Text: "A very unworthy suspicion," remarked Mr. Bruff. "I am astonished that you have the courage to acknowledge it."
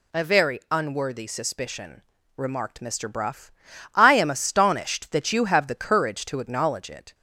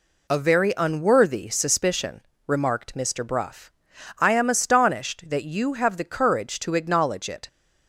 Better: neither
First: none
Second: none

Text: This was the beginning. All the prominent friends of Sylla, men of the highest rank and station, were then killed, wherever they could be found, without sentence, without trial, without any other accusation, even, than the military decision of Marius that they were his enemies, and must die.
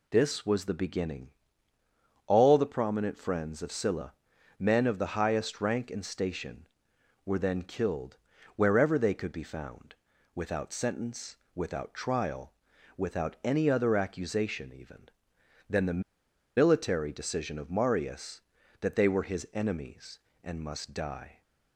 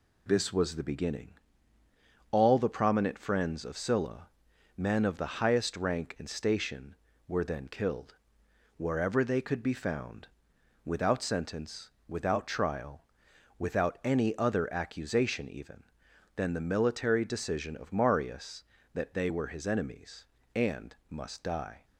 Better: second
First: pauses between "the" and "military"; noticeable; at 16.0 s; 0.56 s long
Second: none

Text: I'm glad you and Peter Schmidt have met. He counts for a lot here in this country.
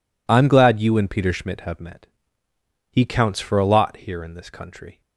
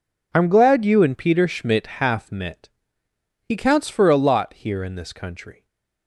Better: first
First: none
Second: says "half" for "have"; at 1.9 s // stays silent after the last word; slight; from 5.5 s on; 0.5 s long

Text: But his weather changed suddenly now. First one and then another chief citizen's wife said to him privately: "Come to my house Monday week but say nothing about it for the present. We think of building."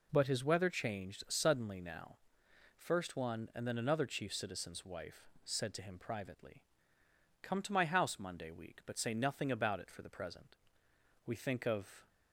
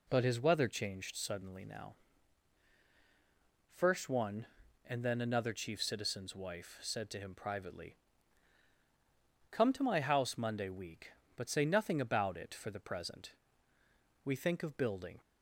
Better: second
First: pauses between "wife" and "said"; slight; at 5.2 s; 0.16 s long // stops before "building"; at 12.0 s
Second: none

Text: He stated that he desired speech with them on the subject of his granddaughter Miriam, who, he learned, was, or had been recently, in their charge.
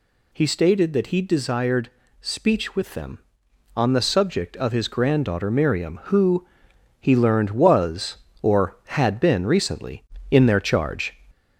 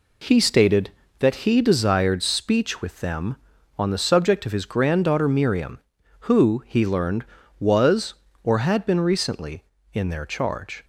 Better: second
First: gets louder; slight; throughout; 2.5 dB // pauses between "desired" and "speech"; slight; at 1.9 s; 0.30 s long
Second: none

